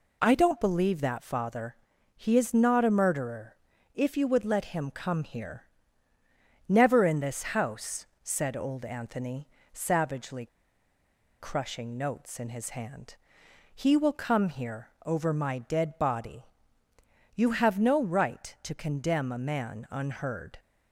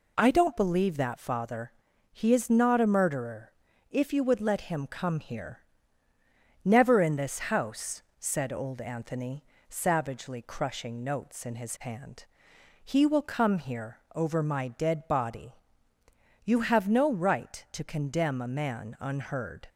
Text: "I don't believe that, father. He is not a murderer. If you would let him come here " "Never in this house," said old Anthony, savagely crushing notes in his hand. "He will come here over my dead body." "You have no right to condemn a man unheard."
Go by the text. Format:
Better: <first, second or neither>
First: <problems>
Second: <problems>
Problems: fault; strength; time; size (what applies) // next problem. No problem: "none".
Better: second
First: pauses between "savagely" and "crushing"; noticeable; at 10.4 s; 0.92 s long // pauses between "here" and "over"; slight; at 14.8 s; 0.16 s long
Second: pauses between "here" and "over"; slight; at 13.9 s; 0.16 s long